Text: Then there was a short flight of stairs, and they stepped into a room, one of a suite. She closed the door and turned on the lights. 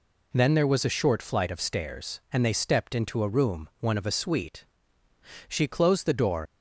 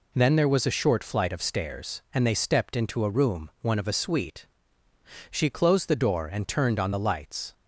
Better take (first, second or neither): second